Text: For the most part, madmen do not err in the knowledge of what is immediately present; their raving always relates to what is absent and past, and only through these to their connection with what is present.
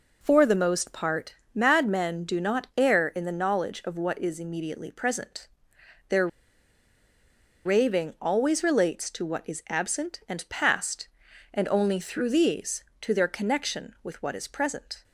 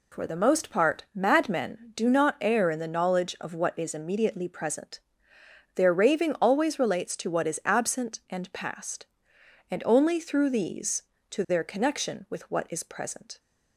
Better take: second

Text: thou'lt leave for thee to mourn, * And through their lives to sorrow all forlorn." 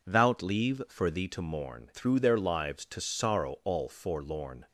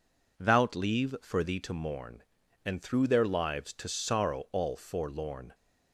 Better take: second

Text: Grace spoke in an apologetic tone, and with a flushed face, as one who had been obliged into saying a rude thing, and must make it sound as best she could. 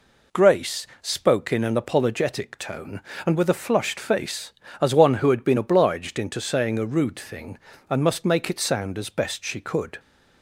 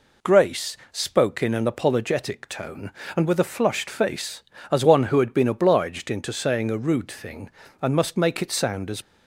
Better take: first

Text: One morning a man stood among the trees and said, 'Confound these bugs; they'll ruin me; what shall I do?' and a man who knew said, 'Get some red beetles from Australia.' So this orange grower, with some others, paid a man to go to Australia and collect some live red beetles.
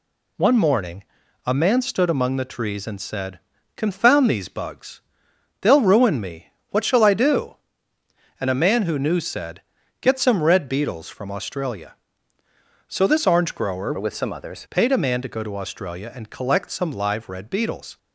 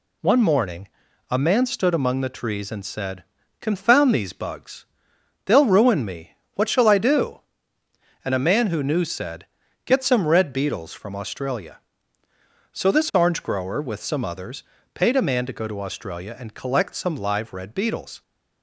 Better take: second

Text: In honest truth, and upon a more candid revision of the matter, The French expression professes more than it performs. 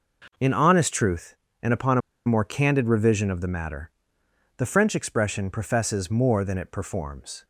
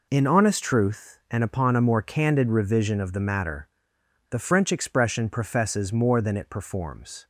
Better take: second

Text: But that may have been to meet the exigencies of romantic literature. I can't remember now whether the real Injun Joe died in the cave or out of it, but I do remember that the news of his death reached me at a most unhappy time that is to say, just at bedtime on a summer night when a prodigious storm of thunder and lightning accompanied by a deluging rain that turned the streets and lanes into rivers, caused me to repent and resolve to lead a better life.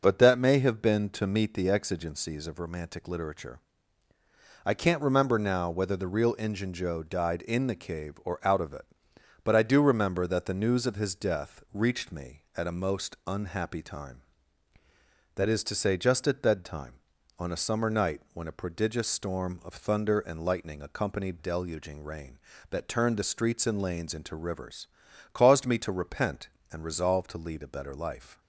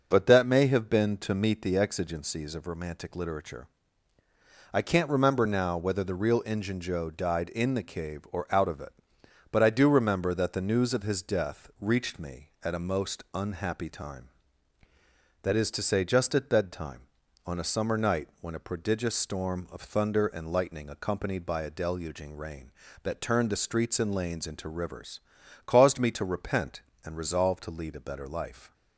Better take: second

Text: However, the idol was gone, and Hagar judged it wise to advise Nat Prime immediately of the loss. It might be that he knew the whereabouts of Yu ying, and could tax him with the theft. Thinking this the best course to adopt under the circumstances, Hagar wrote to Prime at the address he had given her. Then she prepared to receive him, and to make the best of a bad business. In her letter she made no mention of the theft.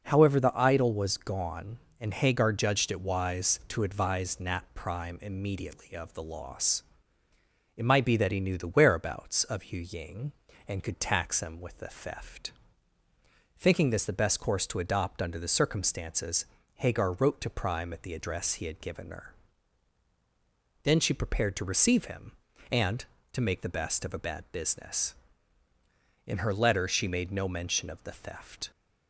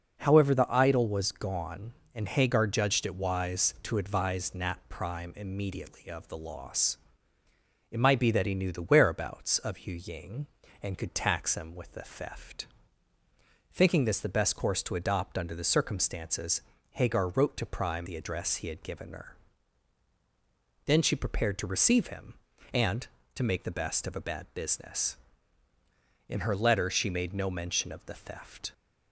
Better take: first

